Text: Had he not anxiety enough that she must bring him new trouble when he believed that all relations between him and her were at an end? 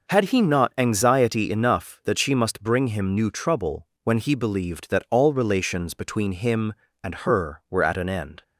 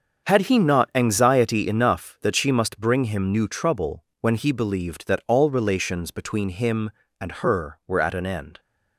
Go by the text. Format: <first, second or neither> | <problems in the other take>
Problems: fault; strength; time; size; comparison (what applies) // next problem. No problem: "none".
first | gets quieter; strong; throughout; 10.5 dB // pauses between "trouble" and "when"; slight; at 4.0 s; 0.18 s long; slight in the first